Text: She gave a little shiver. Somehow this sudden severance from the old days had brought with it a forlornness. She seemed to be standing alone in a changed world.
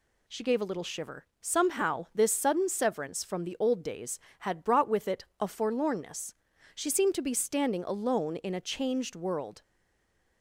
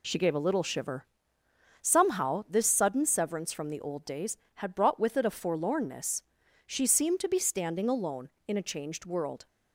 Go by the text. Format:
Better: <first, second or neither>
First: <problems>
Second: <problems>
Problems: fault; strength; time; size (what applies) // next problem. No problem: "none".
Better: second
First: pauses between "it" and "a"; slight; at 5.2 s; 0.16 s long // stays silent after the last word; slight; from 9.6 s on; 0.8 s long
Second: none